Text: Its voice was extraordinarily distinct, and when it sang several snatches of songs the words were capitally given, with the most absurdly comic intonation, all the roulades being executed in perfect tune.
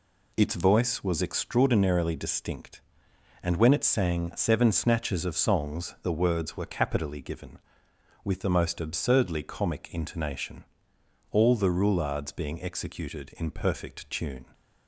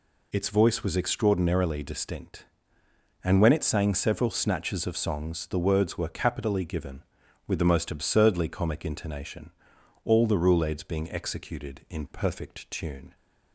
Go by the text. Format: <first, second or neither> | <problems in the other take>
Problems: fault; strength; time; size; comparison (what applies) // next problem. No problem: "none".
second | says "seven" for "several"; at 4.3 s